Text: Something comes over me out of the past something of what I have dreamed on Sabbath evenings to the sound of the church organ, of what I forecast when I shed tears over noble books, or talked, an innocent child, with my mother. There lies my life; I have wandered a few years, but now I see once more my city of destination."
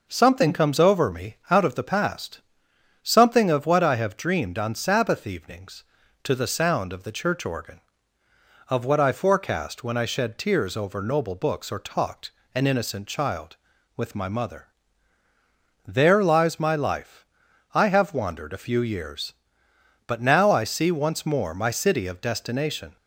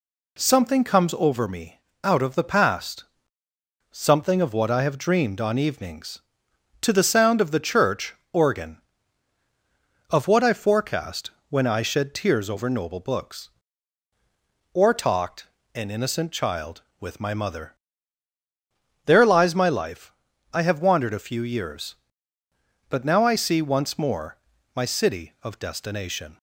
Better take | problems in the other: first | pauses between "me" and "out"; slight; at 1.7 s; 0.24 s long // pauses between "past" and "something"; noticeable; at 3.0 s; 0.84 s long; noticeable in the first // skips "Sabbath"; at 5.5 s // pauses between "church" and "organ"; slight; at 8.1 s; 0.20 s long // pauses between "forecast" and "when"; slight; at 11.3 s; 0.18 s long // pauses between "more" and "my"; at 24.3 s; 0.38 s long

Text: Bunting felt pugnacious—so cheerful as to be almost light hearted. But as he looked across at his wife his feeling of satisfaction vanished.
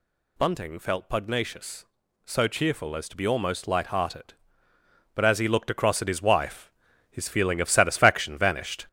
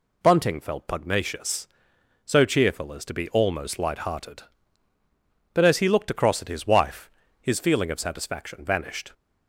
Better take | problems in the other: second | gets louder; noticeable; throughout; 6 dB // pauses between "wife" and "his"; at 6.6 s; 0.40 s long; slight in the second

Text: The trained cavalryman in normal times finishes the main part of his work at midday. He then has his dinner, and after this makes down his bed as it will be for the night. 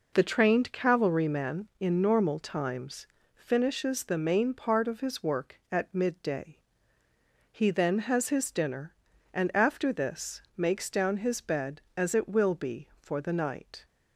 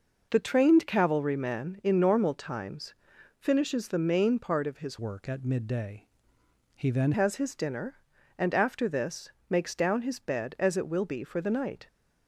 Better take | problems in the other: first | pauses between "times" and "finishes"; noticeable; at 2.9 s; 0.46 s long; slight in the first // changes voice from "work" to "then"; from 4.9 to 7.1 s; 2.2 s long // pauses between "this" and "makes"; slight; at 9.3 s; 0.18 s long; slight in the first

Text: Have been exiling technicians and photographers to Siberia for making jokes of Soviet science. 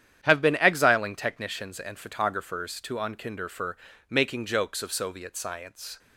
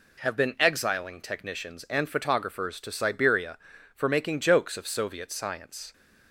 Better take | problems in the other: second | starts louder than the rest; strong; until 1.2 s; 10 dB // says "Unkinder" for "Siberia"; at 3.0 s // pauses between "for" and "making"; slight; at 3.7 s; 0.32 s long

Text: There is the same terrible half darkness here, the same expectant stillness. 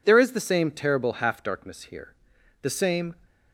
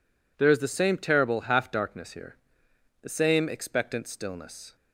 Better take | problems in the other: second | stops before "expectant stillness"; at 3.2 s

